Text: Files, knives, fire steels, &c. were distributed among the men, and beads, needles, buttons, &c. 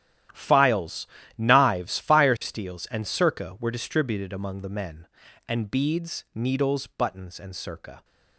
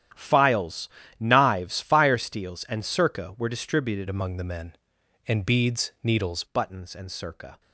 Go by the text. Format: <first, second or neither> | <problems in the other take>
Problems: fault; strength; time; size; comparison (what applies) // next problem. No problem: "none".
first | starts louder than the rest; strong; until 1.4 s; 10.5 dB; strong in the first // changes voice from "among" to "needles"; from 4.0 to 6.4 s; 2.4 s long